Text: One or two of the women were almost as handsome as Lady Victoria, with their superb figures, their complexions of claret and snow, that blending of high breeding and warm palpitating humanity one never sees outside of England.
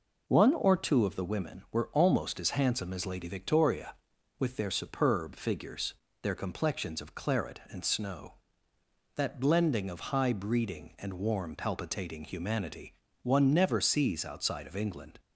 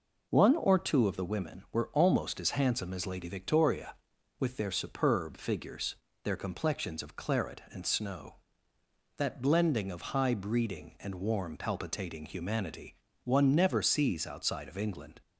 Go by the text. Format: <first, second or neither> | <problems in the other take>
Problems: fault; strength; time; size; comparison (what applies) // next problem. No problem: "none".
neither | pauses between "humanity" and "one"; slight; the same in both